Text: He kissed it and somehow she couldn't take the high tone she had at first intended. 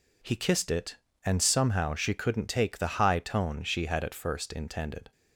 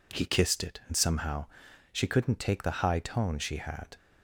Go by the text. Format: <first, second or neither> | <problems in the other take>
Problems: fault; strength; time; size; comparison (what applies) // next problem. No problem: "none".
first | pauses between "somehow" and "she"; noticeable; at 1.4 s; 0.46 s long // stops before "at first intended"; at 3.9 s